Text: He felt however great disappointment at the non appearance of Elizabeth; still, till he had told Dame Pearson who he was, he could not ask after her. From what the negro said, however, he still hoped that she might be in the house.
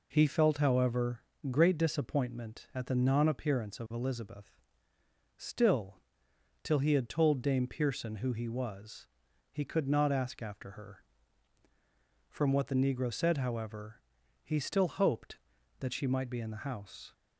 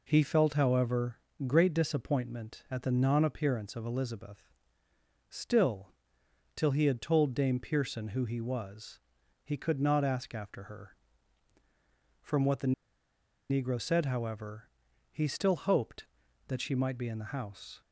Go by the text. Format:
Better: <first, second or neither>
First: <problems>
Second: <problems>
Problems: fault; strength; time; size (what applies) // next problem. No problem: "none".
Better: first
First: pauses between "however" and "great"; slight; at 1.2 s; 0.30 s long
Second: pauses between "however" and "great"; slight; at 1.1 s; 0.30 s long // pauses between "the" and "negro"; noticeable; at 12.7 s; 0.78 s long